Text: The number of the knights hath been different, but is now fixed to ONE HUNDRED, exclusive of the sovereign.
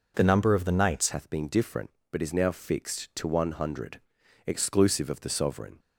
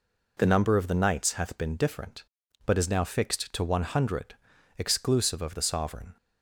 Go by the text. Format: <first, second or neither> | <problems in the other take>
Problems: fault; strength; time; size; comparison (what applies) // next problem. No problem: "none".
second | changes voice at "hath"; from 1.1 s on; 4.6 s long